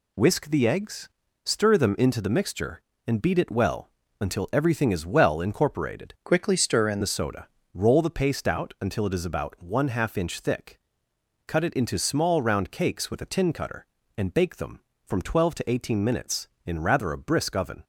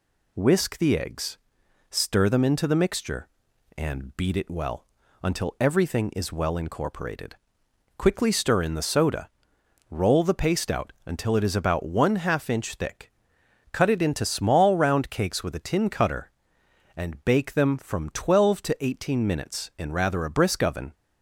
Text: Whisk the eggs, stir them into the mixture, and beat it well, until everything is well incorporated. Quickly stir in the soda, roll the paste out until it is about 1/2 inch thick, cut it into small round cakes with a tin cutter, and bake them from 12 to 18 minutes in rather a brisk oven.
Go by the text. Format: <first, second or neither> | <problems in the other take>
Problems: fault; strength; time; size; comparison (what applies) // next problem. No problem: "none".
second | changes voice from "Quickly" to "in"; from 6.2 to 6.9 s; 0.7 s long